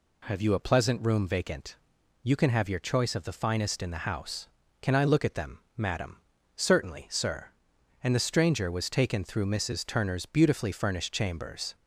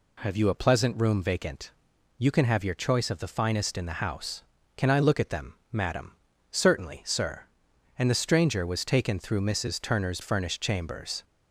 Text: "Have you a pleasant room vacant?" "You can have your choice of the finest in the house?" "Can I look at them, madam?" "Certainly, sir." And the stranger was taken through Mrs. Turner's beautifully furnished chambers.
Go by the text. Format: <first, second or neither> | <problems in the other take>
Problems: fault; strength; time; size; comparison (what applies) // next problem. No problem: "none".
first | skips "beautifully"; at 10.2 s